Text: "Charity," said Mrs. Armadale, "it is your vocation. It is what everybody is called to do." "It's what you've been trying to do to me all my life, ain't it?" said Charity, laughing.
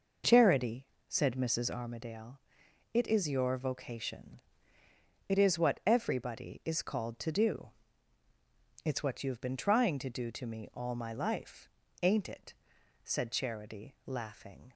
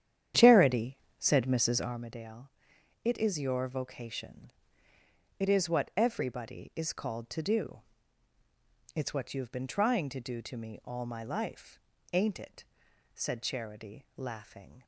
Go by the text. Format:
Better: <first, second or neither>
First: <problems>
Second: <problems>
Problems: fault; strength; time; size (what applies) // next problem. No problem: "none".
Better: first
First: none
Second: starts louder than the rest; strong; until 2.0 s; 9.5 dB